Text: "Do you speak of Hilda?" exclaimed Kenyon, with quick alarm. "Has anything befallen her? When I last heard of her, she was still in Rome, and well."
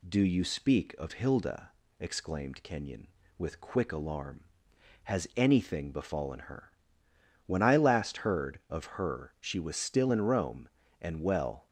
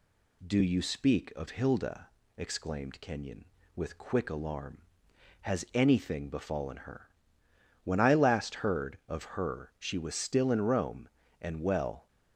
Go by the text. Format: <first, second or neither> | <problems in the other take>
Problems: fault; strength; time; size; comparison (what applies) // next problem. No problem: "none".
neither | none